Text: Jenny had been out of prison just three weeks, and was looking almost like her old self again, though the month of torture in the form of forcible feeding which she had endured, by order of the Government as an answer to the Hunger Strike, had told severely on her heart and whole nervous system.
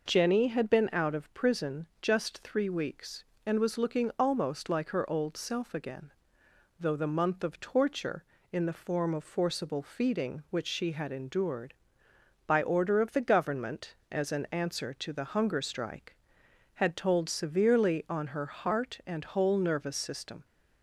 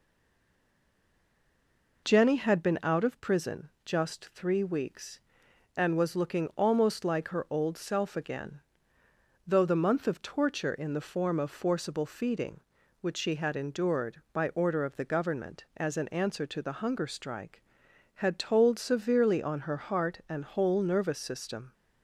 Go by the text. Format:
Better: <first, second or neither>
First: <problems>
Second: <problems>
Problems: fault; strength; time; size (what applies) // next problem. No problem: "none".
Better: first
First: pauses between "prison" and "just"; slight; at 1.8 s; 0.16 s long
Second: stays silent before the first word; noticeable; until 2.0 s; 2.0 s long // pauses between "prison" and "just"; slight; at 3.6 s; 0.16 s long